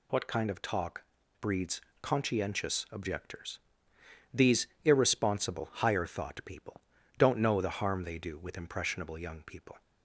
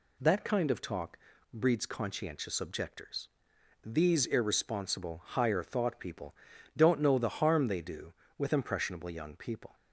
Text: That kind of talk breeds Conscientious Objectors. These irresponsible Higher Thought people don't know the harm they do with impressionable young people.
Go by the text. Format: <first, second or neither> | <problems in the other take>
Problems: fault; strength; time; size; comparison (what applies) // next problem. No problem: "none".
second | says "What" for "That"; at 0.1 s // pauses between "talk" and "breeds"; slight; at 1.0 s; 0.36 s long; slight in the second // pauses between "breeds" and "Conscientious"; slight; at 1.8 s; 0.20 s long // pauses between "These" and "irresponsible"; slight; at 4.6 s; 0.16 s long // pauses between "people" and "don't"; slight; at 6.8 s; 0.36 s long; also in the second